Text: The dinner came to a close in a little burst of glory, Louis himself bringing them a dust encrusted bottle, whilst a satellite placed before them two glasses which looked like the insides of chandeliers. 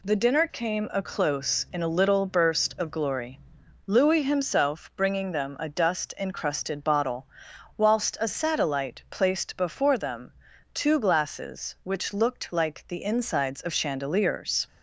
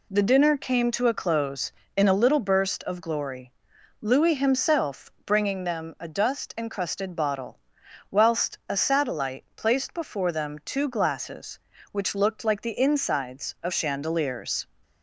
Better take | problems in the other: second | skips "to"; at 0.9 s // pauses between "them" and "two"; at 10.3 s; 0.42 s long

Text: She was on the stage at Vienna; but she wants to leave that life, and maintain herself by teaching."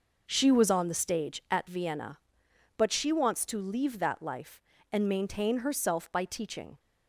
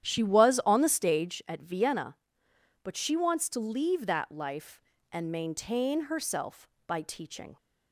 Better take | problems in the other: first | starts louder than the rest; strong; until 1.5 s; 10.5 dB

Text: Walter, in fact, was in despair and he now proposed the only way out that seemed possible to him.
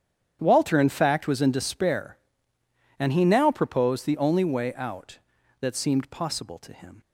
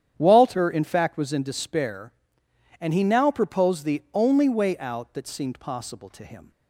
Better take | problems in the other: neither | starts louder than the rest; strong; the same in both

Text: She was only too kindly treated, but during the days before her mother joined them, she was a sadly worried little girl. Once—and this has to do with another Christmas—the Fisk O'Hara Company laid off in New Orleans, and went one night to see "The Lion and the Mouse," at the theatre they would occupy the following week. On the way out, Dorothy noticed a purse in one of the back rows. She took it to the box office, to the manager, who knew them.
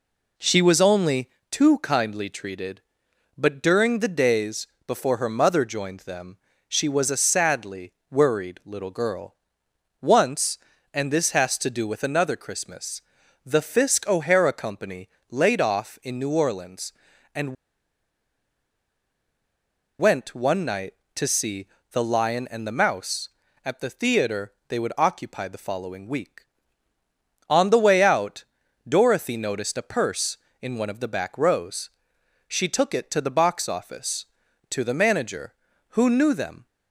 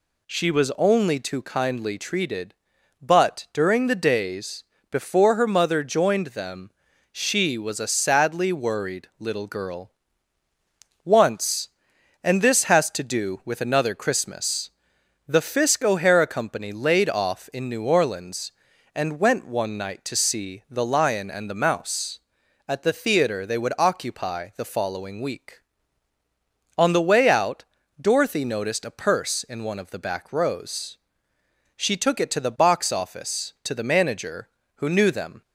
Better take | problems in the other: second | pauses between "only" and "too"; slight; at 1.2 s; 0.22 s long // pauses between "days" and "before"; slight; at 4.6 s; 0.20 s long; slight in the second // pauses between "sadly" and "worried"; slight; at 7.9 s; 0.18 s long // pauses between "Company" and "laid"; slight; at 15.0 s; 0.22 s long // pauses between "and" and "went"; strong; at 17.5 s; 2.4 s long // pauses between "see" and "The"; slight; at 21.6 s; 0.26 s long // pauses between "theatre" and "they"; slight; at 24.5 s; 0.16 s long

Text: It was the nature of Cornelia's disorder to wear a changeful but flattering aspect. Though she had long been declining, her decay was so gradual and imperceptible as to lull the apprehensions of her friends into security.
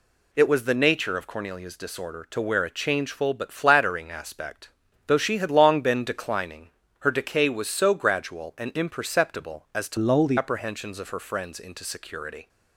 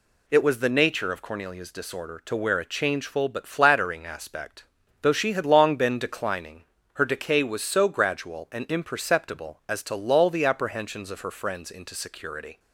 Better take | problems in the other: second | changes voice from "lull" to "the"; from 9.9 to 10.3 s; 0.4 s long

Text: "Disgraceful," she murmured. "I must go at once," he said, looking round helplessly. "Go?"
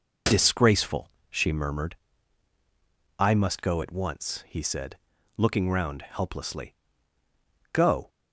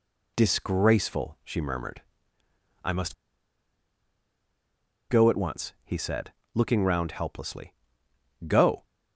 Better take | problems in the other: first | pauses between "must" and "go"; strong; at 3.1 s; 1.9 s long

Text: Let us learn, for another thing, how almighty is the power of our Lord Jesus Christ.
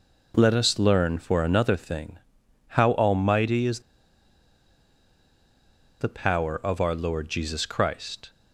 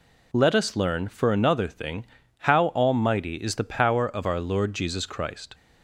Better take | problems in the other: second | pauses between "is" and "the"; strong; at 3.7 s; 2.2 s long

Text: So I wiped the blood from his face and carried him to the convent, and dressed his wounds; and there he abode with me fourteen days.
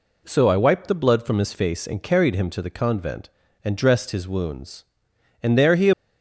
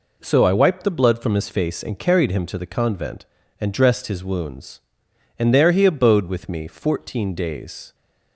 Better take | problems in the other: second | stops before "abode with me fourteen days"; at 5.9 s

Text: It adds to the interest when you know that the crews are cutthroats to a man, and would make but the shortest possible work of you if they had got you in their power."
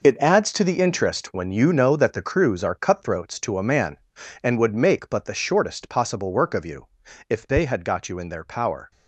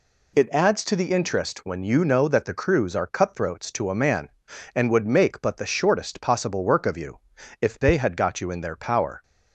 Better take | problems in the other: second | gets quieter; strong; throughout; 10.5 dB // pauses between "you" and "if"; at 6.8 s; 0.40 s long; also in the second

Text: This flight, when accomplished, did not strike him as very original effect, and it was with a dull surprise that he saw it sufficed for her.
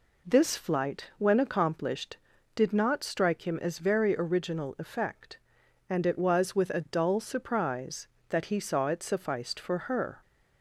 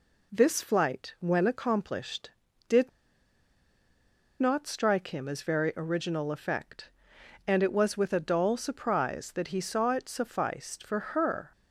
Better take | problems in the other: first | pauses between "did" and "not"; strong; at 2.8 s; 1.5 s long

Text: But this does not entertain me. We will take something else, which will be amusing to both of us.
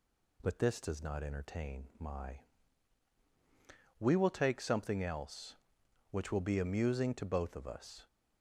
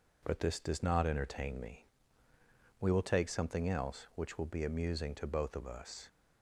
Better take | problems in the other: second | says "my" for "me"; at 1.9 s

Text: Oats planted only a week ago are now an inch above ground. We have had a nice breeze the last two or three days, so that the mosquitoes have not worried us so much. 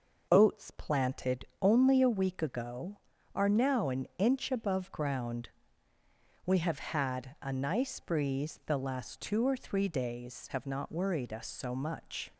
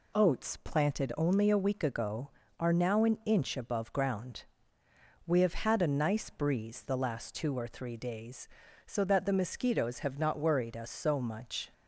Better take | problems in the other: second | pauses between "planted" and "only"; slight; at 1.4 s; 0.16 s long // skips "so that the mosquitoes"; at 10.4 s

